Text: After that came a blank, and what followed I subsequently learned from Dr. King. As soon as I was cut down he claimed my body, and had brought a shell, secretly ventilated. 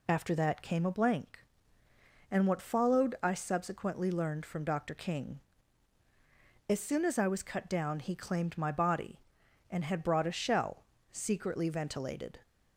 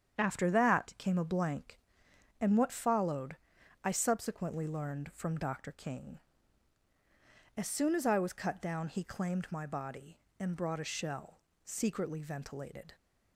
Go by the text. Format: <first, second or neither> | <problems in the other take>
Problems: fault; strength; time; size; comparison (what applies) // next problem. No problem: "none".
first | starts louder than the rest; strong; until 1.2 s; 8.5 dB // pauses between "followed" and "I"; noticeable; at 3.3 s; 0.46 s long // skips "had"; at 10.5 s